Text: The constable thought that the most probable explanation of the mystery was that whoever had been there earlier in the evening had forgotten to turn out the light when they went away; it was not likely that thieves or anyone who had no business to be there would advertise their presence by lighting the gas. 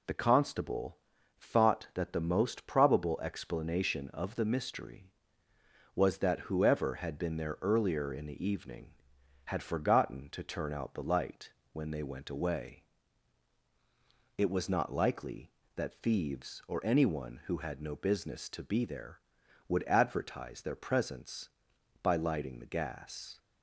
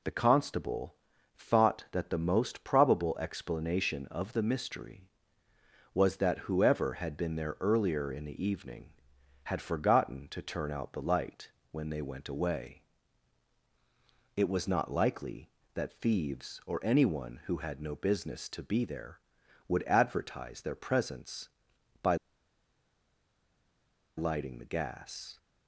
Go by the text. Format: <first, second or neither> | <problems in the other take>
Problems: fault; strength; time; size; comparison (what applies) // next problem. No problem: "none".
first | pauses between "constable" and "thought"; at 0.9 s; 0.40 s long; also in the first // pauses between "light" and "when"; slight; at 11.5 s; 0.20 s long; slight in the first // pauses between "by" and "lighting"; strong; at 22.1 s; 2.0 s long